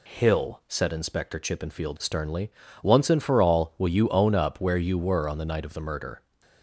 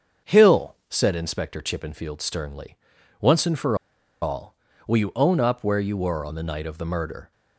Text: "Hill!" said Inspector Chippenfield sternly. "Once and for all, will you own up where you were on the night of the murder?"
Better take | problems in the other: first | starts louder than the rest; until 1.3 s; 7 dB // pauses between "for" and "all"; at 3.7 s; 0.45 s long

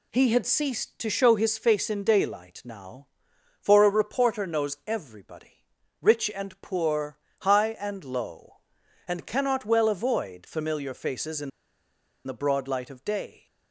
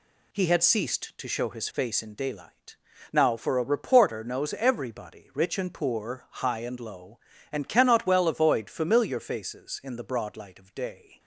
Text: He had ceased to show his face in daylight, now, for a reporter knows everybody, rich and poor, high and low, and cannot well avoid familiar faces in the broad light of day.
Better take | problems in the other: second | pauses between "in" and "the"; noticeable; at 11.5 s; 0.77 s long

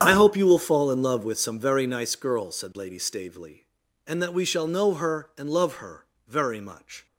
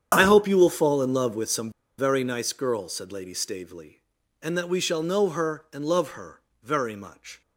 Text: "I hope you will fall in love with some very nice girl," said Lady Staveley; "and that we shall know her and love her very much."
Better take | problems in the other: first | starts louder than the rest; strong; until 1.1 s; 8.5 dB; strong in the first // pauses between "some" and "very"; slight; at 1.7 s; 0.27 s long // pauses between "her" and "very"; slight; at 6.3 s; 0.24 s long; slight in the first

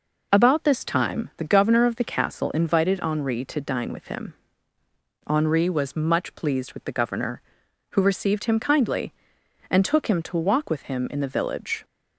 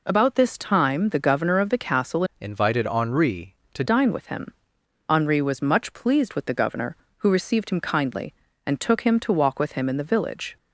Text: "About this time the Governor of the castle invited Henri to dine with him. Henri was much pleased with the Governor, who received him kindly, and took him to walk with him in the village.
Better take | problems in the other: first | changes voice from "invited" to "to"; from 2.3 to 3.8 s; 1.5 s long

